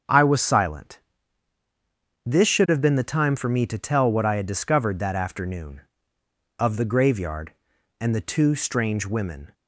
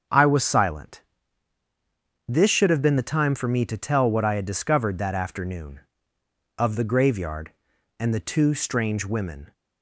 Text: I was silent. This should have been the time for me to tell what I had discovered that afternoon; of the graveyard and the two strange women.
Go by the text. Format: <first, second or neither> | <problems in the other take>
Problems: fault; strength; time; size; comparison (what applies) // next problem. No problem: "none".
neither | starts louder than the rest; the same in both